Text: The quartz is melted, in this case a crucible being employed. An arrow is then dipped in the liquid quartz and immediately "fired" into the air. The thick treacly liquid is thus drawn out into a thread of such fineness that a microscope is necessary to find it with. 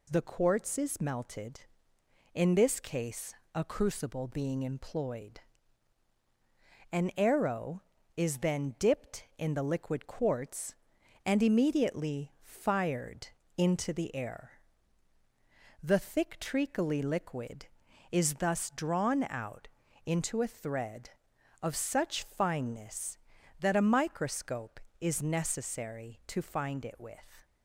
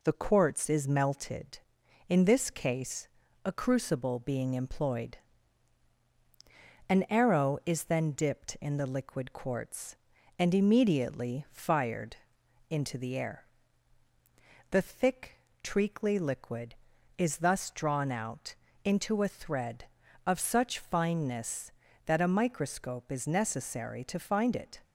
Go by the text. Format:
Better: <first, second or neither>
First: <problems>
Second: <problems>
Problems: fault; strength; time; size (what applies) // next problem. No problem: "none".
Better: first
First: pauses between "case" and "a"; slight; at 3.3 s; 0.20 s long // pauses between "fired" and "into"; slight; at 13.2 s; 0.32 s long // pauses between "out" and "into"; at 19.6 s; 0.38 s long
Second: pauses between "case" and "a"; at 3.0 s; 0.38 s long // pauses between "fired" and "into"; noticeable; at 12.1 s; 0.54 s long // pauses between "thick" and "treacly"; slight; at 15.3 s; 0.24 s long // pauses between "out" and "into"; slight; at 18.5 s; 0.28 s long // stops before "with"; at 24.8 s